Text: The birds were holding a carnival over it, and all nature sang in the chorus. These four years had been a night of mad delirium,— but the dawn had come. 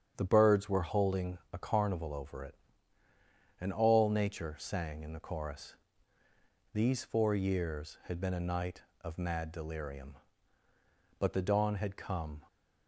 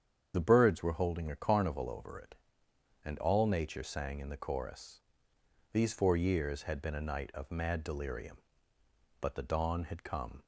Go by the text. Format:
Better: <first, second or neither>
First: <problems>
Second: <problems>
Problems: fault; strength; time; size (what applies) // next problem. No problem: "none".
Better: first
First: starts louder than the rest; strong; until 1.1 s; 8 dB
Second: loses the start of "The"; at 0.3 s; 60 ms // starts louder than the rest; strong; until 1.3 s; 8 dB